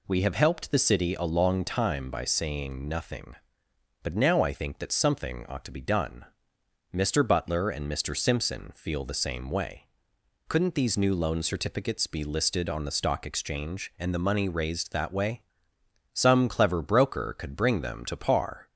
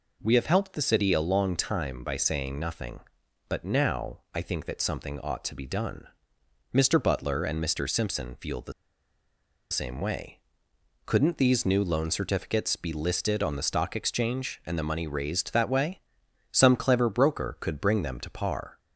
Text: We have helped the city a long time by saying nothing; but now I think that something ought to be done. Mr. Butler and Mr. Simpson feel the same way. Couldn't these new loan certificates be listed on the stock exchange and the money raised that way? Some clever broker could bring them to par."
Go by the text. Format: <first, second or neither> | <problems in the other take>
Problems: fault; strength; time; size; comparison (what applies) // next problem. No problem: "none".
first | pauses between "the" and "same"; at 8.7 s; 0.99 s long